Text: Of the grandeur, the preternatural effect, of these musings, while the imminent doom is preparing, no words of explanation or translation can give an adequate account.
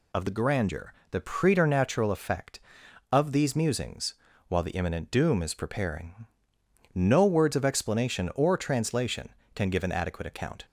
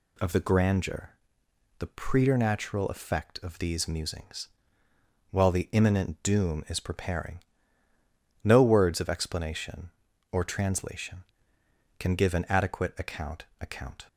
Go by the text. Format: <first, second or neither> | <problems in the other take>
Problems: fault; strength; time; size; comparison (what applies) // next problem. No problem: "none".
first | says "account" twice; at 13.6 s